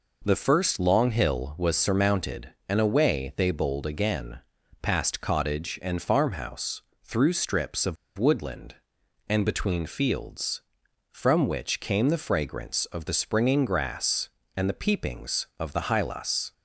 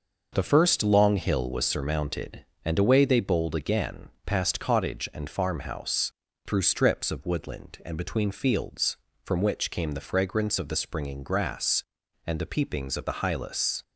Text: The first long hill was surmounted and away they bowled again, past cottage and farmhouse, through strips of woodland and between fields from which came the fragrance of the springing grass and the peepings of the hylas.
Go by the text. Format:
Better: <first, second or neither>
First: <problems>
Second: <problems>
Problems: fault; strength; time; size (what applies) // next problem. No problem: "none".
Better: second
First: pauses between "of" and "woodland"; slight; at 7.9 s; 0.23 s long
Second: none